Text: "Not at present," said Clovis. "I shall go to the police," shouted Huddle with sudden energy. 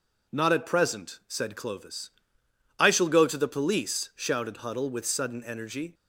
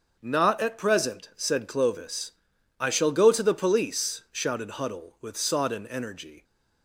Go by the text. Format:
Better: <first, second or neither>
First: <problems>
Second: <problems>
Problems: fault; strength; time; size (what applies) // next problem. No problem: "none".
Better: first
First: none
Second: starts louder than the rest; until 1.2 s; 6.5 dB // says "sodden" for "sudden"; at 5.3 s